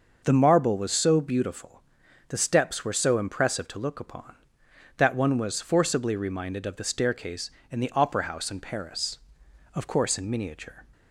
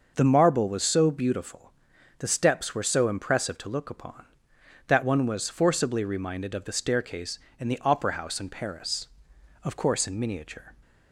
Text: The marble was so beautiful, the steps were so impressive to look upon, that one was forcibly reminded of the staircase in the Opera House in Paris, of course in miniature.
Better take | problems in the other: neither | none

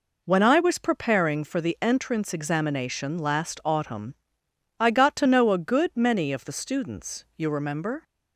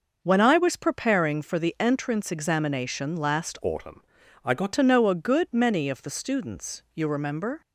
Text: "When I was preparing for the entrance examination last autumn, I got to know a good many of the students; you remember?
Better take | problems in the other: first | changes voice from "autumn" to "got"; from 3.6 to 4.7 s; 1.1 s long

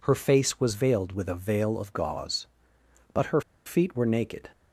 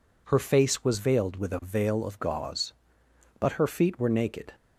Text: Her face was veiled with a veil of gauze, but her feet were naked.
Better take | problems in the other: second | pauses between "her" and "feet"; slight; at 3.4 s; 0.25 s long

